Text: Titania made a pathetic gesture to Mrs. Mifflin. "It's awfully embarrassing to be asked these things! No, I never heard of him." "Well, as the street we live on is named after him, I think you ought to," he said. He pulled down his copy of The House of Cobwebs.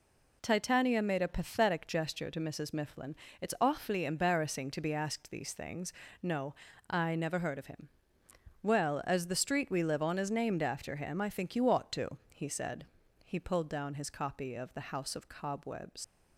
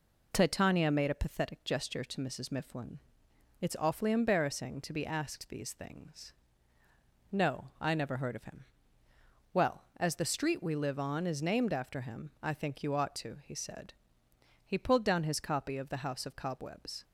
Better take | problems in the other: second | leaves "Cobwebs" unfinished; at 16.0 s; 85 ms

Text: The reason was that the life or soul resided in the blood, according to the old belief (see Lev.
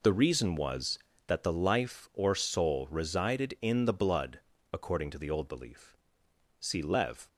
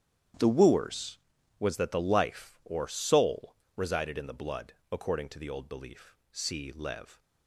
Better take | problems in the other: first | starts louder than the rest; strong; until 1.8 s; 10 dB // says "wooers" for "reason"; at 0.4 s // pauses between "soul" and "resided"; slight; at 3.5 s; 0.22 s long

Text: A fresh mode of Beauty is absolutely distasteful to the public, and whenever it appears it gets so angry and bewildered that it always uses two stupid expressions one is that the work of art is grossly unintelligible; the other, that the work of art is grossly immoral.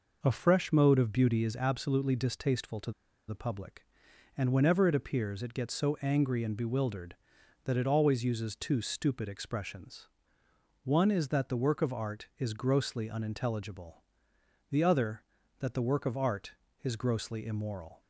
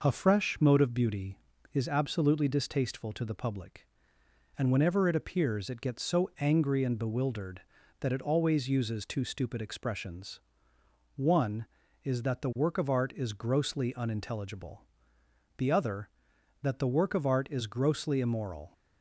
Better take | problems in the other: second | pauses between "to" and "the"; at 2.9 s; 0.37 s long // pauses between "expressions" and "one"; noticeable; at 10.0 s; 0.76 s long; noticeable in the second

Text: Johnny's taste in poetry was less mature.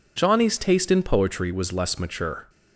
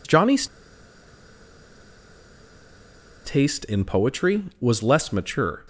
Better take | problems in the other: first | pauses between "Johnny's" and "taste"; strong; at 0.4 s; 2.7 s long

